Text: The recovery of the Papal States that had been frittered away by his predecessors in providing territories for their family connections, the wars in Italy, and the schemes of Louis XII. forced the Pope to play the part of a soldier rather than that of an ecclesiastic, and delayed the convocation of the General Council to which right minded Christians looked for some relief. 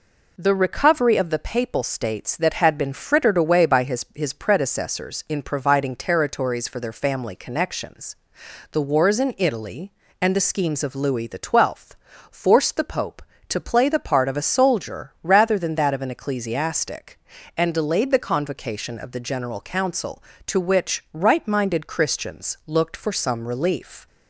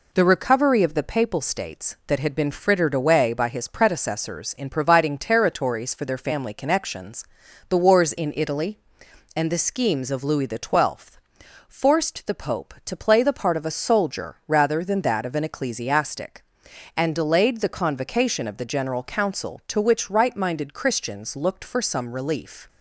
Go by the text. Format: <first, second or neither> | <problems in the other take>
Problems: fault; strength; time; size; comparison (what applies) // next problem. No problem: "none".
second | says "his" twice; at 4.1 s